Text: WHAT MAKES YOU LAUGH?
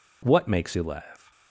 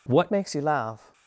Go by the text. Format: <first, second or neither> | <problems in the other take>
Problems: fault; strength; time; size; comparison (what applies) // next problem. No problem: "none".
first | changes voice at "MAKES"; from 0.2 s on; 0.9 s long